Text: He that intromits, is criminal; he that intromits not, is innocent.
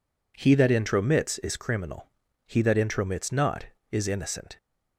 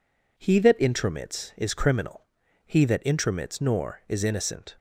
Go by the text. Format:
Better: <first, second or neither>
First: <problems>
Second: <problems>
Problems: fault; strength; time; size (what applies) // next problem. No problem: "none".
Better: first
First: none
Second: says "nor" for "not"; at 3.5 s